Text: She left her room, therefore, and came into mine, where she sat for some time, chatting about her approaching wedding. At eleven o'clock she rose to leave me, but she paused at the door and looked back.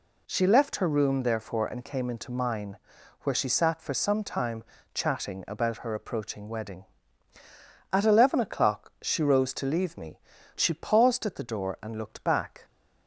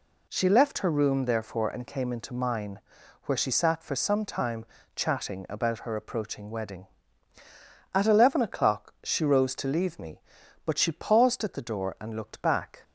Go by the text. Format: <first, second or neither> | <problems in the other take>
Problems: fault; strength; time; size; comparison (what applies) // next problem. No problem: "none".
second | skips "but"; at 10.3 s